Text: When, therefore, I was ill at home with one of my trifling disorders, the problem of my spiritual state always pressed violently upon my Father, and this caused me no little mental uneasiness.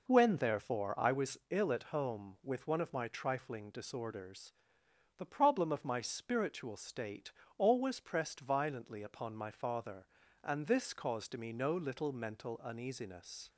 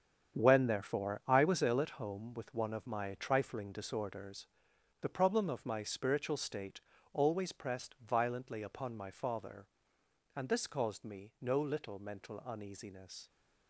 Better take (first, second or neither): first